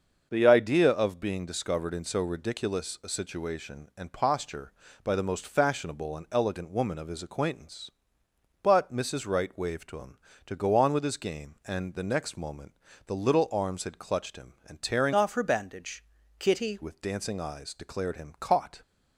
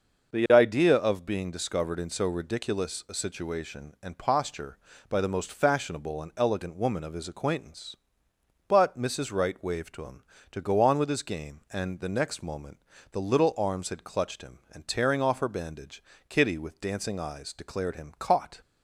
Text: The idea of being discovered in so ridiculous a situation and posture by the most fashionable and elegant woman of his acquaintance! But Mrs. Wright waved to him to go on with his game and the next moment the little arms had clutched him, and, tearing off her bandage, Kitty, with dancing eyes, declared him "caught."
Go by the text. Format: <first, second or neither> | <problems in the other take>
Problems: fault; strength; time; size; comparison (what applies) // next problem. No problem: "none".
second | starts louder than the rest; until 1.3 s; 6.5 dB // pauses between "moment" and "the"; slight; at 12.7 s; 0.34 s long; slight in the second // changes voice from "off" to "Kitty"; from 15.1 to 16.7 s; 1.6 s long